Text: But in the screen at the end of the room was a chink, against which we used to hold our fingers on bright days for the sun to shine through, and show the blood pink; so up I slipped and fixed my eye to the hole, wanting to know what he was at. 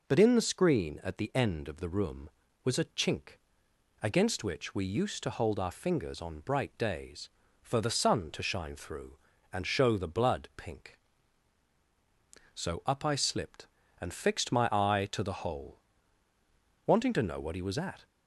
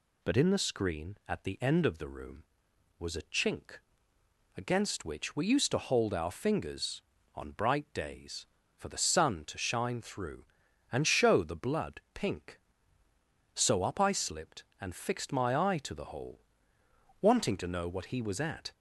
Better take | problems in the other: neither | none

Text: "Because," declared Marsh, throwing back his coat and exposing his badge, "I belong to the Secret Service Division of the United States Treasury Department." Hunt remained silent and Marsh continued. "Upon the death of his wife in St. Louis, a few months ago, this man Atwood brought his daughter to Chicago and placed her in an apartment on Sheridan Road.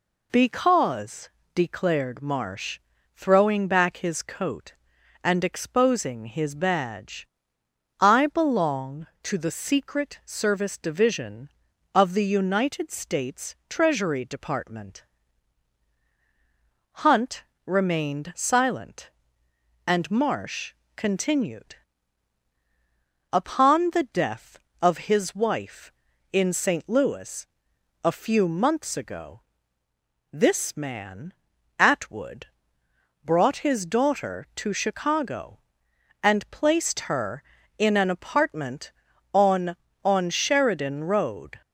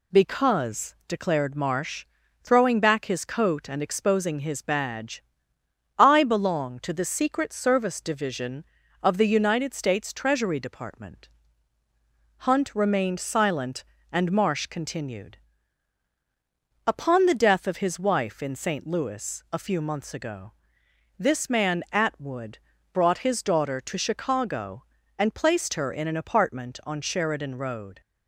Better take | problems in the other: second | pauses between "Hunt" and "remained"; slight; at 17.4 s; 0.22 s long // pauses between "Marsh" and "continued"; slight; at 20.7 s; 0.22 s long // pauses between "man" and "Atwood"; noticeable; at 31.3 s; 0.46 s long // pauses between "Atwood" and "brought"; noticeable; at 32.4 s; 0.78 s long; slight in the second // says "on" twice; at 40.0 s

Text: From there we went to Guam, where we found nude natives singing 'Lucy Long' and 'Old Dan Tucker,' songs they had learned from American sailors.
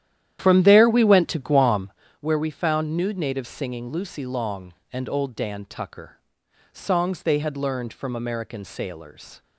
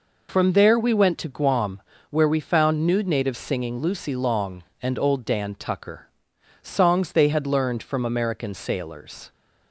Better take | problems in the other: second | starts louder than the rest; strong; until 2.0 s; 11 dB

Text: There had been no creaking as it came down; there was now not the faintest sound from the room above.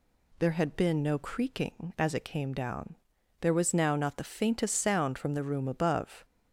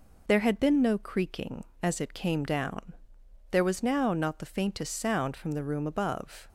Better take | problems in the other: neither | none

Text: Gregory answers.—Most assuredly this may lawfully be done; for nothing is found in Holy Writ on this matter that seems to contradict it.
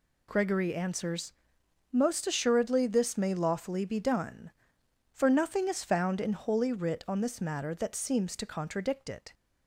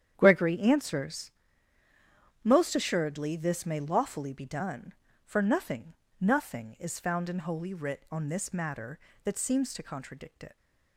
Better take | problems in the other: first | starts louder than the rest; strong; until 1.1 s; 9 dB // says "nothing" twice; at 6.2 s

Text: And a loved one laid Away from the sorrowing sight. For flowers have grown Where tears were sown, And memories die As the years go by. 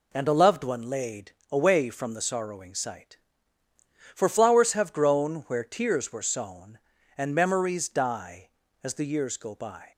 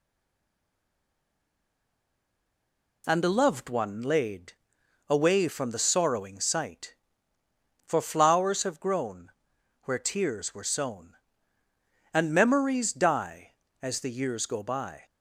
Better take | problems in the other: first | stays silent before the first word; strong; until 3.0 s; 3.0 s long // pauses between "laid" and "Away"; noticeable; at 4.5 s; 0.54 s long; slight in the first // pauses between "grown" and "Where"; noticeable; at 9.2 s; 0.54 s long

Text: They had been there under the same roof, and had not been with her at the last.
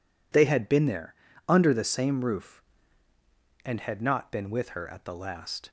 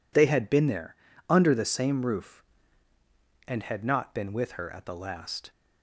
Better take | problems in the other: neither | pauses between "there" and "under"; slight; the same in both

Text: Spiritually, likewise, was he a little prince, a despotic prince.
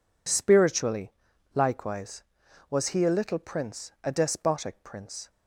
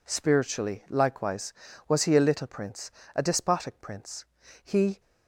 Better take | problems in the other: first | goes on to say "He"; slight; from 4.6 s on; 0.36 s long

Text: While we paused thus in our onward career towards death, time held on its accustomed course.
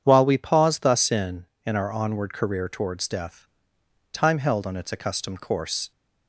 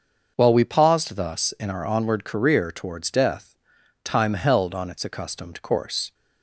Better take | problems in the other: second | starts louder than the rest; strong; until 1.0 s; 8 dB; also in the second // says "in" twice; at 1.6 s

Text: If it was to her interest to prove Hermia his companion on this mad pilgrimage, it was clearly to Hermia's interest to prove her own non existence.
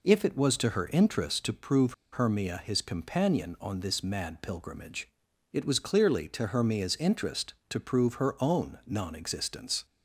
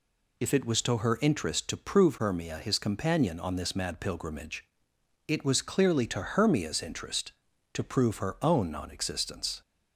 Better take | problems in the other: second | pauses between "prove" and "Hermia"; slight; at 1.9 s; 0.19 s long

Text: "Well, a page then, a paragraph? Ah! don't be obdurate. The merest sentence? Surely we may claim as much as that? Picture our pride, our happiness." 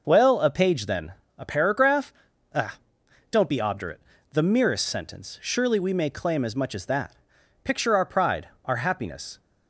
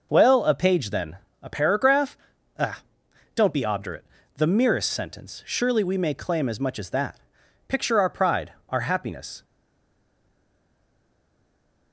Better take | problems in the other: first | stays silent after the last word; from 9.4 s on; 2.5 s long

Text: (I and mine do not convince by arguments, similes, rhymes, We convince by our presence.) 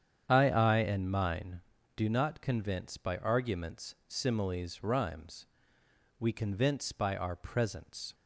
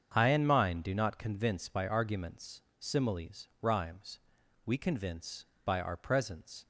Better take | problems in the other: second | starts louder than the rest; strong; until 1.3 s; 8.5 dB; strong in the second // says "I" twice; at 0.4 s

